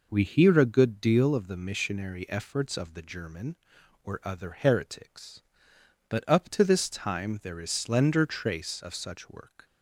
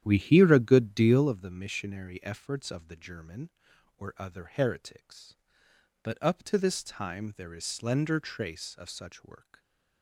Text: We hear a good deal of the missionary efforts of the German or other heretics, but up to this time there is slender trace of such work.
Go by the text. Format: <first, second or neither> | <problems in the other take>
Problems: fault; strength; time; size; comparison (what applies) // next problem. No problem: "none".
first | starts louder than the rest; strong; until 1.5 s; 10.5 dB